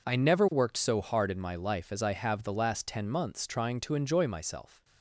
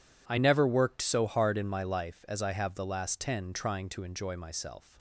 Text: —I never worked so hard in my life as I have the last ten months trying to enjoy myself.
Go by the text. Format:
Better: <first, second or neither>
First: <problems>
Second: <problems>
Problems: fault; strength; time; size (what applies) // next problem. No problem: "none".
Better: first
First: none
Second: skips "months"; at 3.5 s